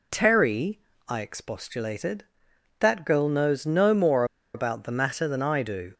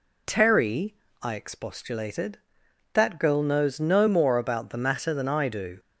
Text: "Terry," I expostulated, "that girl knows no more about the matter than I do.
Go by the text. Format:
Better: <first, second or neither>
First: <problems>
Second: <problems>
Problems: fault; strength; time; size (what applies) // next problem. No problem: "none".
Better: second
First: pauses between "more" and "about"; slight; at 4.2 s; 0.30 s long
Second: none